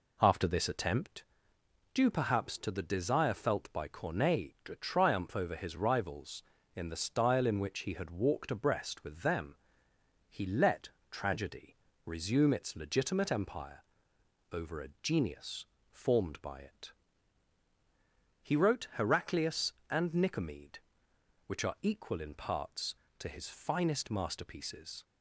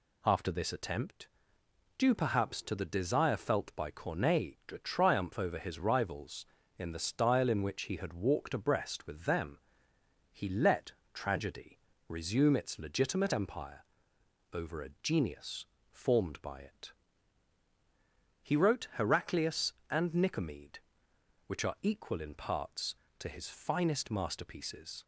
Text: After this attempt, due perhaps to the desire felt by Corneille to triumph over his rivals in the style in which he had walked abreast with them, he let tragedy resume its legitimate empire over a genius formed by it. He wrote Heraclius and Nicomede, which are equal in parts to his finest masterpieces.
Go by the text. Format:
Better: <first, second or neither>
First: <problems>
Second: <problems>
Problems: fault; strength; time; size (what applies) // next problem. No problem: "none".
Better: second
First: starts louder than the rest; slight; until 1.3 s; 3 dB // pauses between "let" and "tragedy"; slight; at 10.8 s; 0.22 s long // pauses between "tragedy" and "resume"; slight; at 11.7 s; 0.28 s long // pauses between "empire" and "over"; noticeable; at 13.8 s; 0.68 s long // pauses between "genius" and "formed"; slight; at 15.6 s; 0.26 s long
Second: pauses between "let" and "tragedy"; slight; at 10.9 s; 0.22 s long // pauses between "tragedy" and "resume"; slight; at 11.7 s; 0.28 s long // pauses between "empire" and "over"; noticeable; at 13.8 s; 0.68 s long // pauses between "genius" and "formed"; slight; at 15.6 s; 0.26 s long